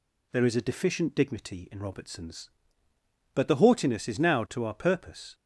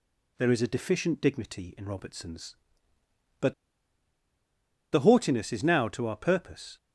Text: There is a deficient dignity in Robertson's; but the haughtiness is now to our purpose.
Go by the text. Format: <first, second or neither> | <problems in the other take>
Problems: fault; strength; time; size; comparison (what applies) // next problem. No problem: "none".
first | pauses between "but" and "the"; strong; at 3.5 s; 1.3 s long